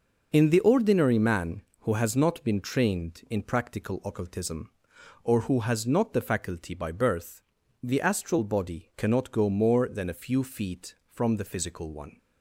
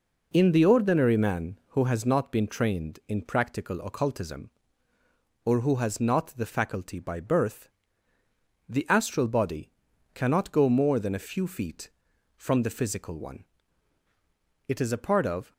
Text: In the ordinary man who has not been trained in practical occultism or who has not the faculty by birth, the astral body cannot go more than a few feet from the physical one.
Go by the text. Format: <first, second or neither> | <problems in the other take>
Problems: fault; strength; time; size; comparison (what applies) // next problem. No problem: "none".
first | pauses between "body" and "cannot"; noticeable; at 9.6 s; 0.46 s long // goes on to say "It is a part of"; noticeable; from 14.6 s on; 0.84 s long